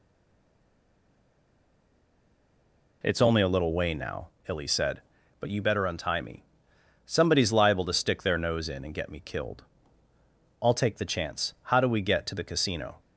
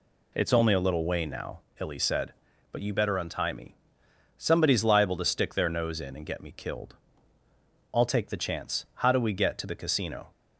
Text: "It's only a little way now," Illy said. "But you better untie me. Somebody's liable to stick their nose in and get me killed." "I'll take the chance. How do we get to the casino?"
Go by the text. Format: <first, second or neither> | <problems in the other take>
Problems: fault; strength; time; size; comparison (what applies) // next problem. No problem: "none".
second | stays silent before the first word; strong; until 3.0 s; 3.0 s long